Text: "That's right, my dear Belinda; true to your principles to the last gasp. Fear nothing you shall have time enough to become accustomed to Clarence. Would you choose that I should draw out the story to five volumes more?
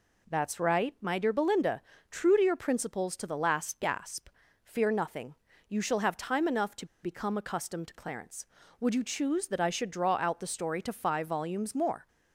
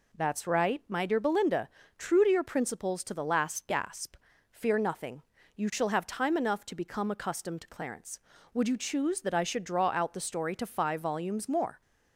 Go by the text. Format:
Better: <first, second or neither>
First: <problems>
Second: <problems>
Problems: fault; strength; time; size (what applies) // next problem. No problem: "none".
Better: second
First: pauses between "nothing" and "you"; slight; at 5.3 s; 0.32 s long // pauses between "to" and "become"; slight; at 6.8 s; 0.17 s long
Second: pauses between "nothing" and "you"; slight; at 5.2 s; 0.32 s long